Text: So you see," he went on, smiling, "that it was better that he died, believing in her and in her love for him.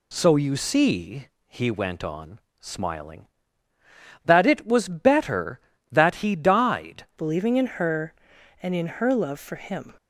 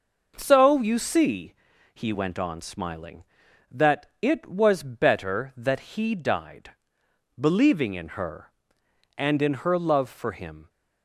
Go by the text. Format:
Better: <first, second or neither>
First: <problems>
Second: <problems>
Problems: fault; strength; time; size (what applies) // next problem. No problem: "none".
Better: second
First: changes voice at "believing"; from 7.1 s on; 2.8 s long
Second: none